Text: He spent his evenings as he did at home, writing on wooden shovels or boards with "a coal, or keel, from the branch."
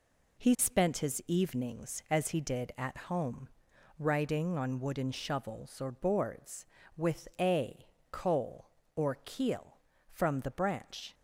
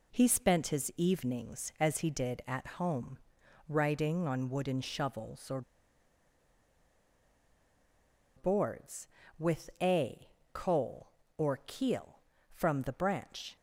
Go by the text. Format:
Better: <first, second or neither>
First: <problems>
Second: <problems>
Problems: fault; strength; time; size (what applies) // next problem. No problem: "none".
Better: first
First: pauses between "a" and "coal"; slight; at 7.8 s; 0.24 s long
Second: pauses between "or" and "boards"; strong; at 5.6 s; 2.7 s long // pauses between "a" and "coal"; slight; at 10.2 s; 0.24 s long